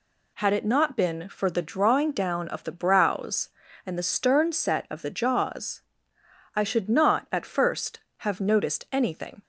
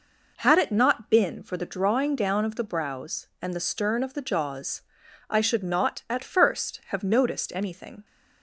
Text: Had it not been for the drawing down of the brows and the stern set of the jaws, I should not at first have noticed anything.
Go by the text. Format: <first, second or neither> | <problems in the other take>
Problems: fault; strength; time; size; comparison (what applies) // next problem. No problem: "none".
first | skips "set"; at 4.0 s